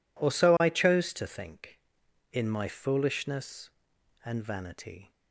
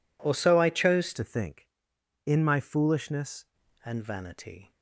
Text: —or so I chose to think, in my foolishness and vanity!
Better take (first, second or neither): first